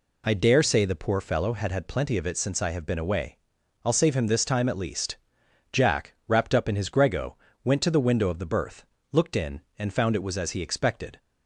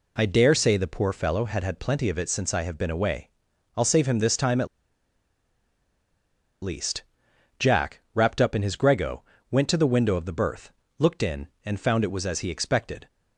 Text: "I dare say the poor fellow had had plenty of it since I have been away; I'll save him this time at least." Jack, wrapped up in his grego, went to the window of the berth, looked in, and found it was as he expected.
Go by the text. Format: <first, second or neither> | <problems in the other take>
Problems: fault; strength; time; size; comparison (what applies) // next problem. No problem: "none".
first | pauses between "at" and "least"; strong; at 4.6 s; 1.9 s long